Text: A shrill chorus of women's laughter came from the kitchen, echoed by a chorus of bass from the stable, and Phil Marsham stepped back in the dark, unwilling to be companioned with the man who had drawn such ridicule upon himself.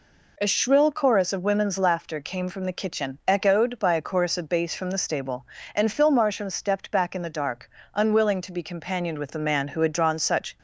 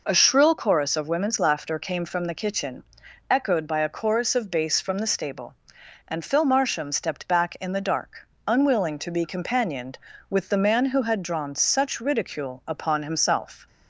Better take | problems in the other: second | stops before "ridicule upon himself"; at 10.5 s

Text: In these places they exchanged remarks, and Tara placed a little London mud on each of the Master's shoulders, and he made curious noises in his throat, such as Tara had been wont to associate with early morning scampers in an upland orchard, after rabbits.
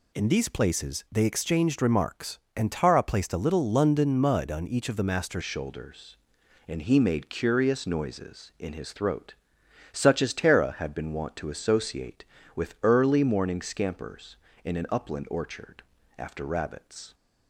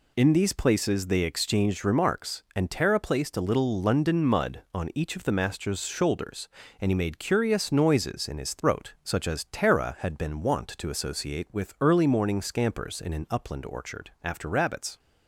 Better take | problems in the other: second | changes voice at "shoulders"; from 5.4 s on; 11.7 s long

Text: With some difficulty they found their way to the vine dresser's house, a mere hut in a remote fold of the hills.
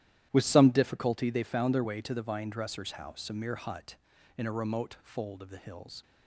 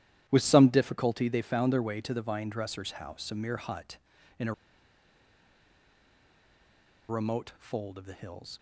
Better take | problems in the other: first | starts louder than the rest; strong; until 1.2 s; 12 dB; strong in the first // pauses between "a" and "remote"; strong; at 4.5 s; 2.5 s long

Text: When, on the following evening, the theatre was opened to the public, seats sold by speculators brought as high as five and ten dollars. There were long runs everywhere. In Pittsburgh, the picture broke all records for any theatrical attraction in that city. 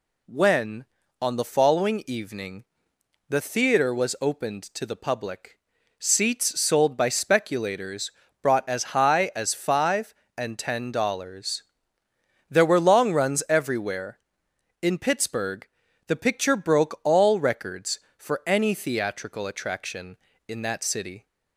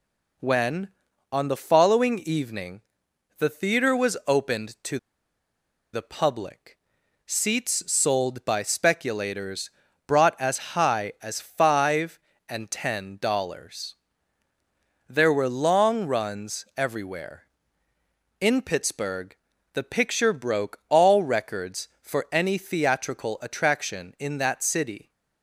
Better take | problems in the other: first | pauses between "to" and "the"; noticeable; at 4.9 s; 0.96 s long // pauses between "speculators" and "brought"; at 9.6 s; 0.38 s long; slight in the first

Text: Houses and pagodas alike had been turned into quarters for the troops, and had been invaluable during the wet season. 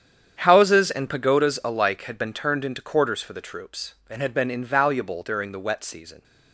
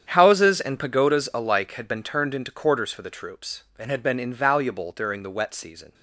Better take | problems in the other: neither | starts louder than the rest; strong; the same in both

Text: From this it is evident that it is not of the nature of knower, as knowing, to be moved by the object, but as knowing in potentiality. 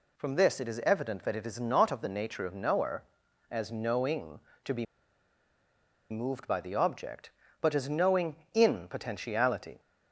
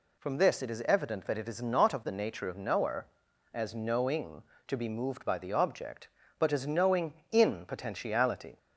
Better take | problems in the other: second | pauses between "be" and "moved"; strong; at 4.8 s; 1.2 s long

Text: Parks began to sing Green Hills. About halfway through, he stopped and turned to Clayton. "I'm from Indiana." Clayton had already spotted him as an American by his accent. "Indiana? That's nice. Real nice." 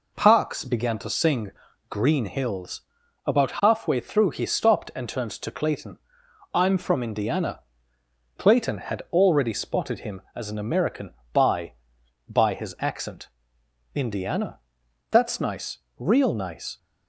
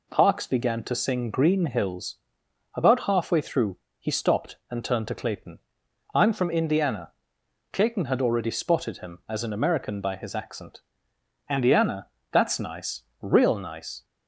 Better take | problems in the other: second | pauses between "sing" and "Green"; at 1.5 s; 0.38 s long // says "by" twice; at 12.2 s

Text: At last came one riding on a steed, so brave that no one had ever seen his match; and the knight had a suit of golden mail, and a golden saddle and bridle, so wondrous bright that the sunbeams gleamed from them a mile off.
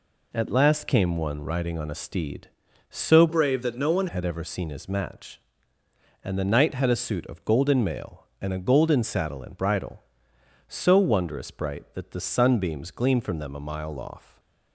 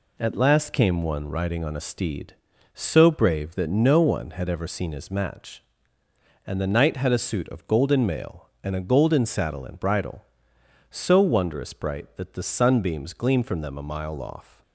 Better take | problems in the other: second | changes voice from "brave" to "one"; from 3.2 to 4.0 s; 0.8 s long // stays silent after the last word; slight; from 14.1 s on; 0.6 s long

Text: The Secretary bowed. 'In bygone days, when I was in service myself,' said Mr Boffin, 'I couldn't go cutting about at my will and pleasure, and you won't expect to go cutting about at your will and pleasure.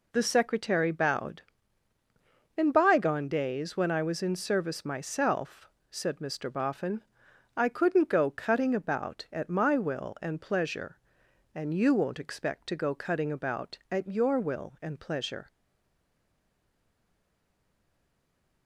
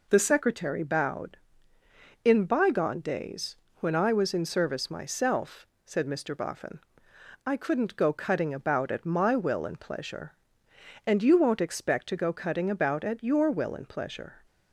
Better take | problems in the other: second | stays silent after the last word; strong; from 15.4 s on; 3.2 s long

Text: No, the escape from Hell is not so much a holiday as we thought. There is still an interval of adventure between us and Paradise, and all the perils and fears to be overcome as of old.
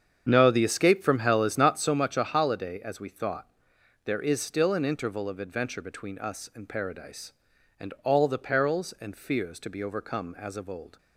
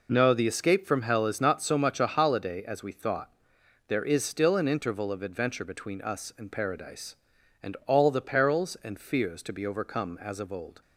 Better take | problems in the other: second | starts louder than the rest; strong; until 2.0 s; 8 dB

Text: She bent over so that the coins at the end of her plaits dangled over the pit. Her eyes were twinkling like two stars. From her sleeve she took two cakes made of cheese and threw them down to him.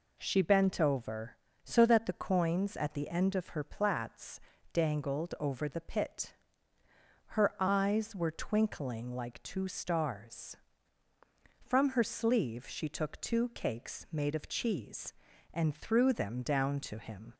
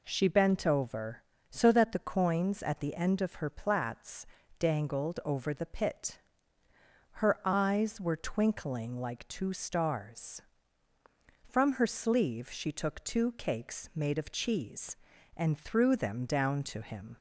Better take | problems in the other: neither | pauses between "plaits" and "dangled"; slight; the same in both

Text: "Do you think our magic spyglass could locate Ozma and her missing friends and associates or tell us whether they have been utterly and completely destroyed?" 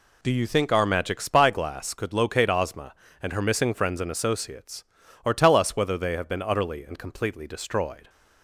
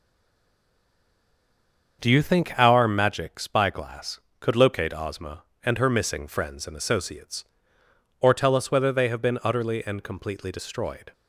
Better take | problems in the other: first | stays silent before the first word; noticeable; until 1.9 s; 1.9 s long // starts louder than the rest; until 3.0 s; 6.5 dB

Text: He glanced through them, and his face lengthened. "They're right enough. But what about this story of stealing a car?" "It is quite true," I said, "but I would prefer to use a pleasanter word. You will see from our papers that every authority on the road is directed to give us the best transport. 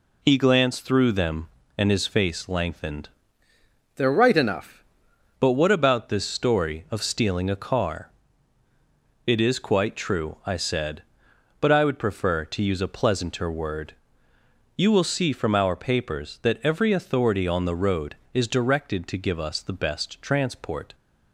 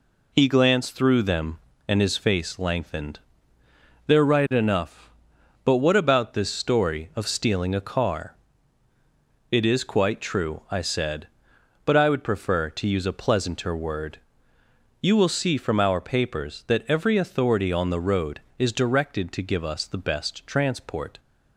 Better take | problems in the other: second | changes voice from "They're" to "enough"; from 3.9 to 4.8 s; 0.9 s long

